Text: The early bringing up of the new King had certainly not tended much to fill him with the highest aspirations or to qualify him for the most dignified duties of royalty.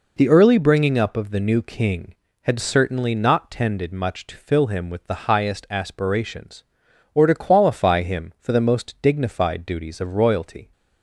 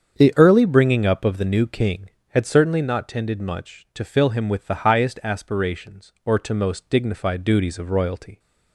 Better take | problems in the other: first | starts louder than the rest; strong; until 1.1 s; 7.5 dB // skips "qualify him for the"; at 6.5 s

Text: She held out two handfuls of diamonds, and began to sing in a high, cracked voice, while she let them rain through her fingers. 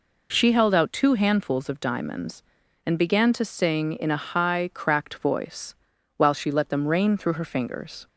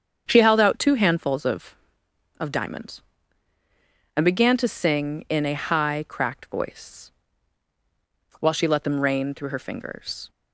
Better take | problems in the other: first | starts louder than the rest; strong; until 1.2 s; 7.5 dB // says "of" twice; at 2.3 s

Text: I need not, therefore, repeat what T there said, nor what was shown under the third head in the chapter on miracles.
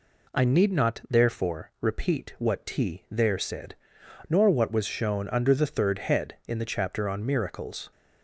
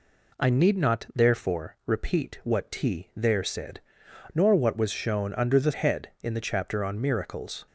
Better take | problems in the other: first | skips "third"; at 5.7 s

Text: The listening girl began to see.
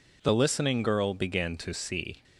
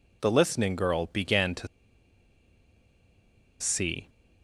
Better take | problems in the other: first | pauses between "to" and "see"; strong; at 1.6 s; 1.9 s long

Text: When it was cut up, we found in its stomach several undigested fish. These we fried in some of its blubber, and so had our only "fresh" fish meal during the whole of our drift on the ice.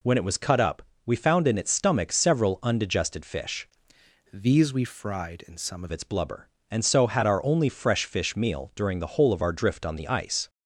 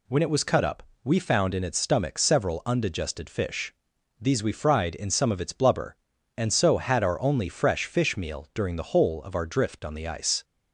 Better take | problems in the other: second | changes voice from "These" to "of"; from 4.3 to 5.9 s; 1.6 s long

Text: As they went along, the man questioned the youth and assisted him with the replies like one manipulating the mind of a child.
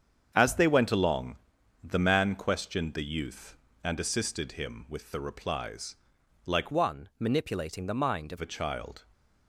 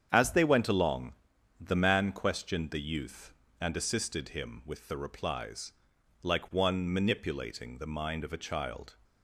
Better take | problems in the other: second | starts louder than the rest; strong; until 1.3 s; 7.5 dB; strong in the second // pauses between "replies" and "like"; noticeable; at 5.9 s; 0.50 s long; noticeable in the second // changes voice from "one" to "of"; from 6.7 to 8.3 s; 1.6 s long

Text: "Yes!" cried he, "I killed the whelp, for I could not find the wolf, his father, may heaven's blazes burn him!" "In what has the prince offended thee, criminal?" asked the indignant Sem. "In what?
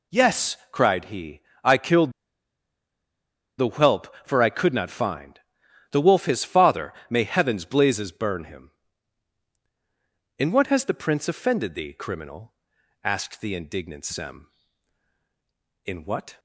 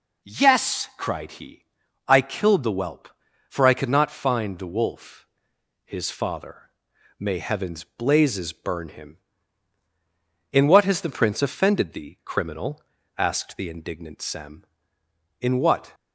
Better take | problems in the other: second | pauses between "killed" and "the"; strong; at 2.1 s; 1.4 s long // pauses between "find" and "the"; noticeable; at 5.3 s; 0.52 s long

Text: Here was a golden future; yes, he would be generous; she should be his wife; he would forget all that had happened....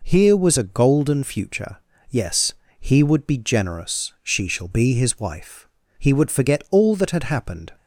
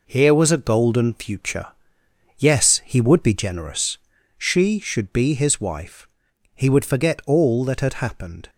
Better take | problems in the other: second | says "shall" for "should"; at 4.4 s

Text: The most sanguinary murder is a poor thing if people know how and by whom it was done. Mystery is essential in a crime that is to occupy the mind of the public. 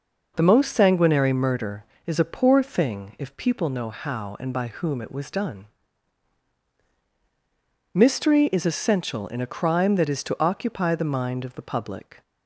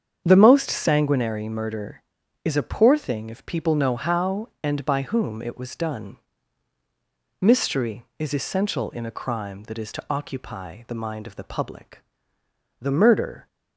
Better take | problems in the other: first | starts louder than the rest; strong; until 1.2 s; 7.5 dB // goes on to say "The murder"; noticeable; from 12.8 s on; 0.66 s long

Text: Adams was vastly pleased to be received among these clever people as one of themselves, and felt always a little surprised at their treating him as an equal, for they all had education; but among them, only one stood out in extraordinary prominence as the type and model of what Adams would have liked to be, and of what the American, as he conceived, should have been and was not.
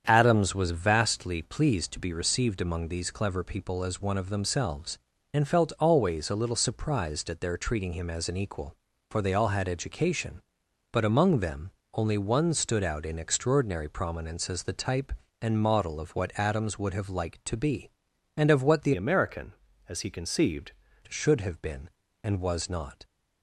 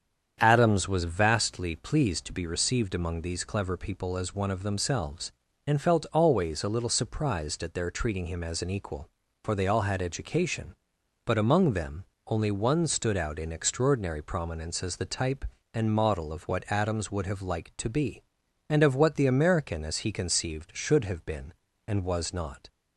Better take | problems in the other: second | starts louder than the rest; strong; until 1.0 s; 8 dB; strong in the second // changes voice from "American" to "conceived"; from 18.9 to 20.7 s; 1.8 s long

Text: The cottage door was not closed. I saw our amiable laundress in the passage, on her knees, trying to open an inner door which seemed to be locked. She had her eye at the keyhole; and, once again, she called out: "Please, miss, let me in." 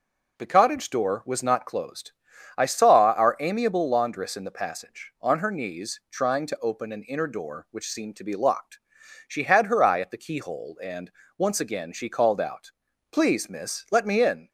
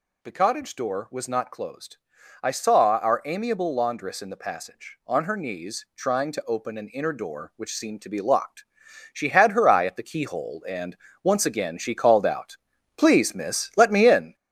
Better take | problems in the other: first | gets louder; noticeable; throughout; 5.5 dB

